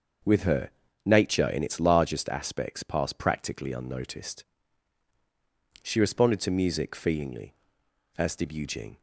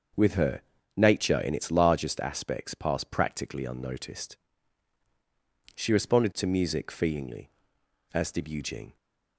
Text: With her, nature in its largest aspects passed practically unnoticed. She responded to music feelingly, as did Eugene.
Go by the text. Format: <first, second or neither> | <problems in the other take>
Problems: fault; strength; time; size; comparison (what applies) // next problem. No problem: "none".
neither | starts louder than the rest; the same in both